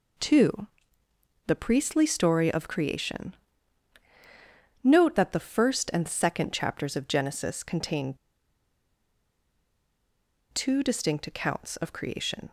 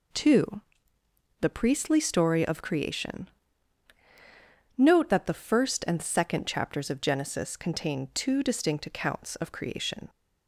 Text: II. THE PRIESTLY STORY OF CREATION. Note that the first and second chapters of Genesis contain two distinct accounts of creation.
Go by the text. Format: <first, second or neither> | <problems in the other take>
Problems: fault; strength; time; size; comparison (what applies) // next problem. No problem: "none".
second | pauses between "contain" and "two"; strong; at 8.1 s; 2.3 s long